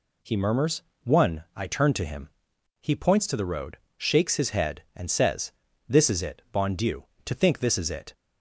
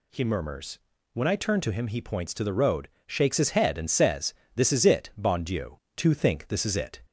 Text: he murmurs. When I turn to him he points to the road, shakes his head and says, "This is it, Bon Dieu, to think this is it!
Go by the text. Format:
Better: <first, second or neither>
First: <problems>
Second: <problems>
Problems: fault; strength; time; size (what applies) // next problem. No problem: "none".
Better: second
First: says "One" for "When"; at 1.0 s // pauses between "him" and "he"; noticeable; at 2.2 s; 0.50 s long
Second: none